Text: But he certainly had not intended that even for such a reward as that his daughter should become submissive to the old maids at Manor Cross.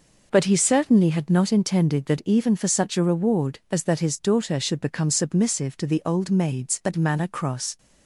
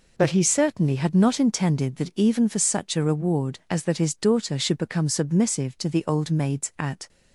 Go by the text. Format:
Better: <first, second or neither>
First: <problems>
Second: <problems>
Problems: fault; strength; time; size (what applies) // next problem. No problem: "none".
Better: first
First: none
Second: stops before "Manor Cross"; at 7.0 s